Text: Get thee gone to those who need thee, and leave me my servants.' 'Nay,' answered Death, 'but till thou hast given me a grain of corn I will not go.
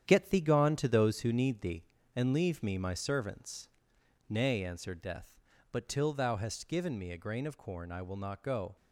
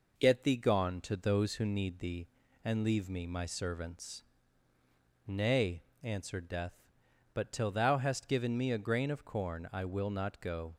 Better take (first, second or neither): second